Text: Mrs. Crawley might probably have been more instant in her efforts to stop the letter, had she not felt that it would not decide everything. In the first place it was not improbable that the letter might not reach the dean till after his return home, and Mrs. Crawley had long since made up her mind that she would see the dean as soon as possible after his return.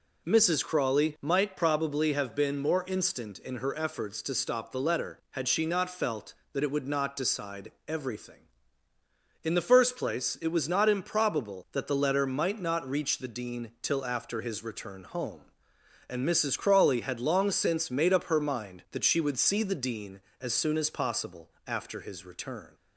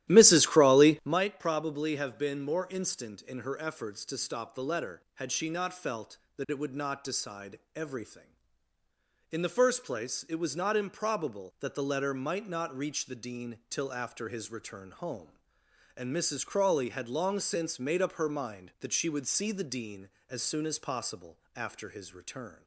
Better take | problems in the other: first | starts louder than the rest; strong; until 1.3 s; 13 dB // pauses between "decide" and "everything"; slight; at 7.5 s; 0.16 s long; slight in the first // pauses between "possible" and "after"; slight; at 21.3 s; 0.18 s long; slight in the first

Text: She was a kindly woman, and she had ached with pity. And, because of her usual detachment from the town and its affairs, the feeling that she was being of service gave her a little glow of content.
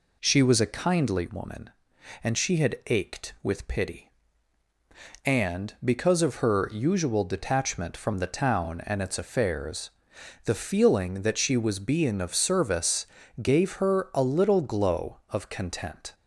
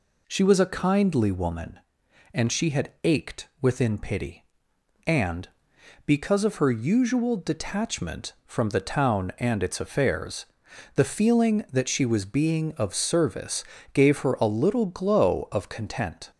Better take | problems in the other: first | says "within" for "with"; at 3.6 s // pauses between "service" and "gave"; slight; at 13.6 s; 0.30 s long; slight in the first

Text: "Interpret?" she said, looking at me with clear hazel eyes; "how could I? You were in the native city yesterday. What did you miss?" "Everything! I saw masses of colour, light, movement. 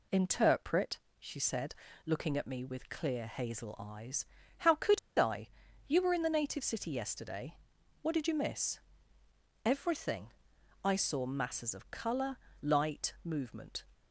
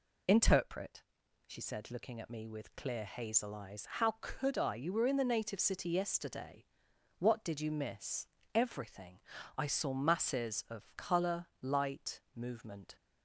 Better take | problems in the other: second | pauses between "could" and "I"; slight; at 4.9 s; 0.19 s long

